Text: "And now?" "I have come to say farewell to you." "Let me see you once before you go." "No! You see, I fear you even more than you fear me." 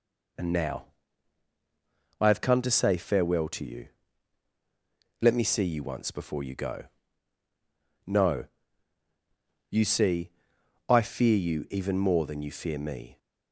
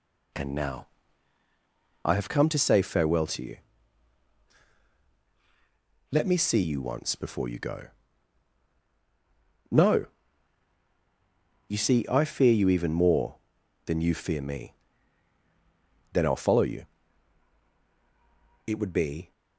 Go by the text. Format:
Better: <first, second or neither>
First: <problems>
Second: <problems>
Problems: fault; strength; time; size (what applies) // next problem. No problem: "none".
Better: first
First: none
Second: goes on to say "Then I'll follow you It would be"; strong; from 16.1 s on; 3.1 s long